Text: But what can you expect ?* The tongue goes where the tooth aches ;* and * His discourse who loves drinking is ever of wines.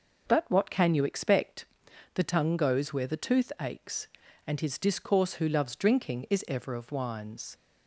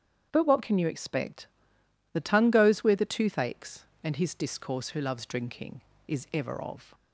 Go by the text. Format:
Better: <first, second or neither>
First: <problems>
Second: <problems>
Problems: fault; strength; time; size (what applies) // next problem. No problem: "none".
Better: first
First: starts louder than the rest; noticeable; until 1.3 s; 6 dB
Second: starts louder than the rest; strong; until 1.3 s; 8.5 dB // stops before "wines"; at 6.9 s